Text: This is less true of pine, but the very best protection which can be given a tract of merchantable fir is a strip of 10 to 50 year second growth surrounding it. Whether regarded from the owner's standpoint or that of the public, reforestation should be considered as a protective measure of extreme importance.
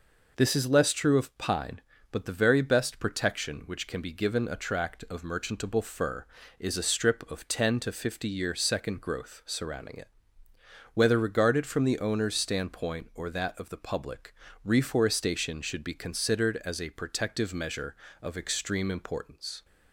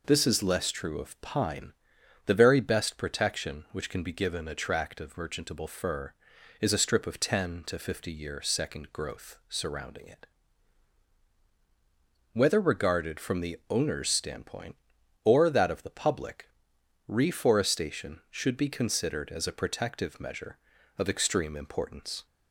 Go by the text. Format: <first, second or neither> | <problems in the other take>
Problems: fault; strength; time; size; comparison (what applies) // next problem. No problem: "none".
first | skips "but"; at 1.9 s